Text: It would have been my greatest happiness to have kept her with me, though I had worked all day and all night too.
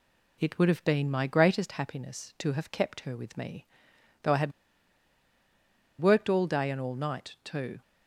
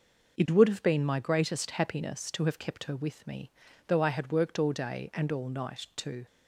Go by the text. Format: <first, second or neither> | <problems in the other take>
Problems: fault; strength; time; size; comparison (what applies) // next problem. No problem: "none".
second | pauses between "had" and "worked"; strong; at 4.5 s; 1.4 s long